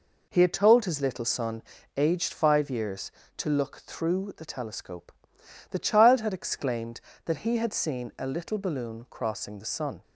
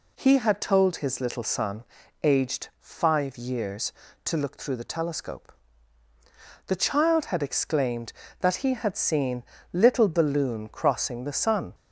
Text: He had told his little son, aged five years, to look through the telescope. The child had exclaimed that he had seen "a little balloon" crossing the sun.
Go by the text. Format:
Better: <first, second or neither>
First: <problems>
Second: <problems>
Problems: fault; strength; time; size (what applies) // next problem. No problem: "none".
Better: first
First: none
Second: skips "a"; at 9.5 s